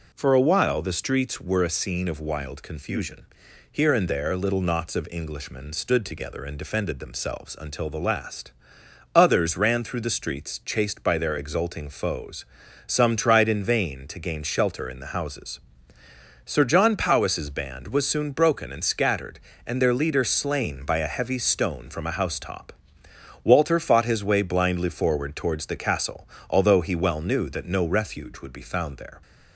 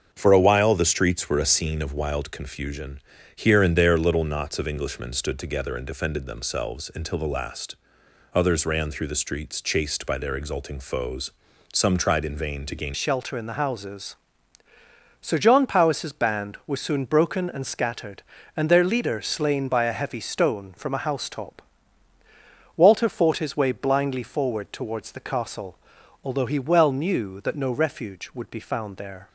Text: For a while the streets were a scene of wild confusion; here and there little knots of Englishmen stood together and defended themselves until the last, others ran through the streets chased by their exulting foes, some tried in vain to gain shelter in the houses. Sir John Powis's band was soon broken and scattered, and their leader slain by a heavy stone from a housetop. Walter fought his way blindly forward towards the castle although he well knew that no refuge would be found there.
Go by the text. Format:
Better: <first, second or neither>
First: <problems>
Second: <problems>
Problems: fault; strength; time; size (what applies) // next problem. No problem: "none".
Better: first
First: pauses between "castle" and "although"; slight; at 26.2 s; 0.20 s long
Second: starts louder than the rest; until 1.1 s; 7 dB // changes voice at "shelter"; from 12.9 s on; 16.3 s long // pauses between "castle" and "although"; noticeable; at 25.7 s; 0.48 s long